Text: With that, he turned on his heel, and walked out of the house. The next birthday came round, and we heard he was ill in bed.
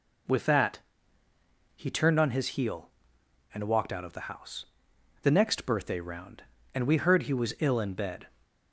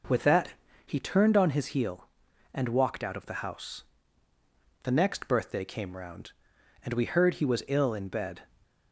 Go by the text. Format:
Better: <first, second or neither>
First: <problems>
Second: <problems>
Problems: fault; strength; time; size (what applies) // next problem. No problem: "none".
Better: second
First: skips "came"; at 5.9 s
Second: none